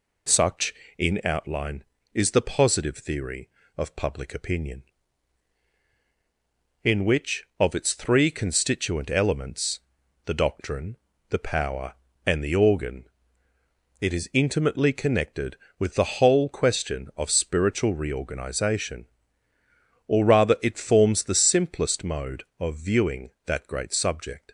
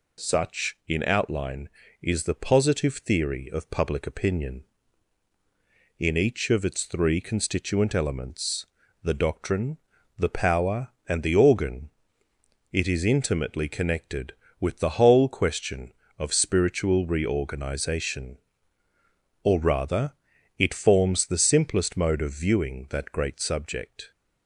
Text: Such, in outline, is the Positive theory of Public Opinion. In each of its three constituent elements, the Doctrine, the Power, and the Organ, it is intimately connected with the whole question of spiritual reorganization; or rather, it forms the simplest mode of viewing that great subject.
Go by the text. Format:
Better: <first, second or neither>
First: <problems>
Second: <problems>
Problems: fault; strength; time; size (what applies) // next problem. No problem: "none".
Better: second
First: says "which" for "each"; at 7.0 s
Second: none